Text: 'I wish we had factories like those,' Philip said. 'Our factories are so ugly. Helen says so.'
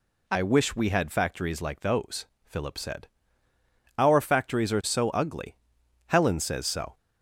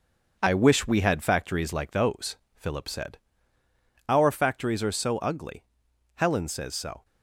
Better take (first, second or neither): first